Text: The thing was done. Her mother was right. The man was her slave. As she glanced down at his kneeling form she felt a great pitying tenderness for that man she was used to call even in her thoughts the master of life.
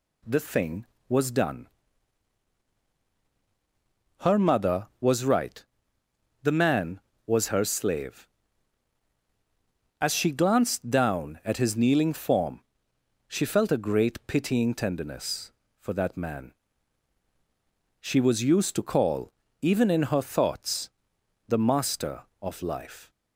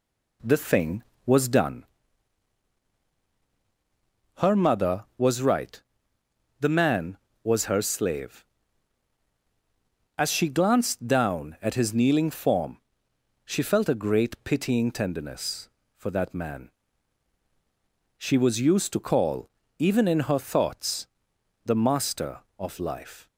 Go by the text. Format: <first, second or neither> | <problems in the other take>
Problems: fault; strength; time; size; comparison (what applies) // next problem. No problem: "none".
first | starts louder than the rest; slight; until 1.9 s; 2.5 dB // pauses between "form" and "she"; noticeable; at 12.7 s; 0.66 s long; noticeable in the first // pauses between "man" and "she"; strong; at 16.6 s; 1.5 s long; strong in the first // pauses between "call" and "even"; slight; at 19.4 s; 0.30 s long; slight in the first // pauses between "thoughts" and "the"; noticeable; at 21.0 s; 0.58 s long; noticeable in the first